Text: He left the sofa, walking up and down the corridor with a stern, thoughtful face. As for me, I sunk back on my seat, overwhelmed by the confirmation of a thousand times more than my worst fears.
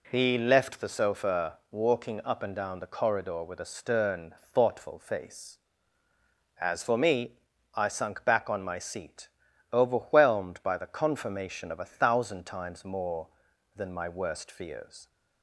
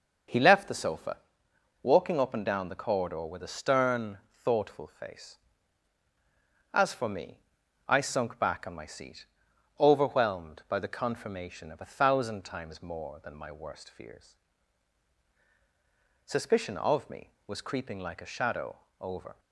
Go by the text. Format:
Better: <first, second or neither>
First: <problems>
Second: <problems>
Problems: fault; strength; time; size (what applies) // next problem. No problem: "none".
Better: first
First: none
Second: goes on to say "Suspicion of me was creeping like a shadow over"; strong; from 16.2 s on; 3.1 s long